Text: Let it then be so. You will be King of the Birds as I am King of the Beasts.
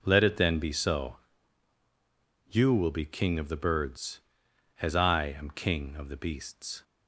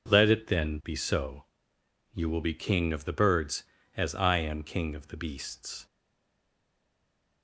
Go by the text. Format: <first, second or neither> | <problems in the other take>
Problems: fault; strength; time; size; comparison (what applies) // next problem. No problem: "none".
first | stays silent after the last word; noticeable; from 5.8 s on; 1.6 s long